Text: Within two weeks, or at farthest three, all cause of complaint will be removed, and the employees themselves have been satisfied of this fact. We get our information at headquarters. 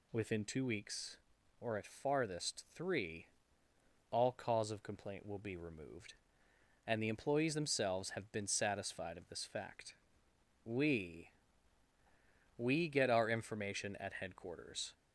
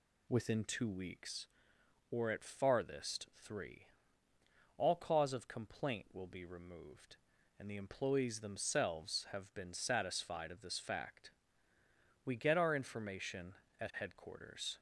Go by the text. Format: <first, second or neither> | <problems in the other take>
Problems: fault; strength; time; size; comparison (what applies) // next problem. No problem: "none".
second | says "We" twice; at 12.5 s